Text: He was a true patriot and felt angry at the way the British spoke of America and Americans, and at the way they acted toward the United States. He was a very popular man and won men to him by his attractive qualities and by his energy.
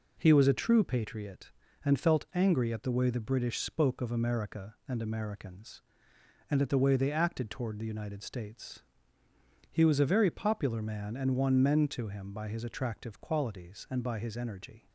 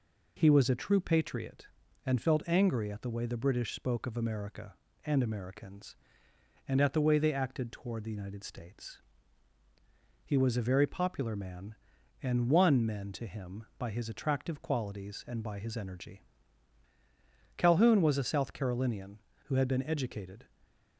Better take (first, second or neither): first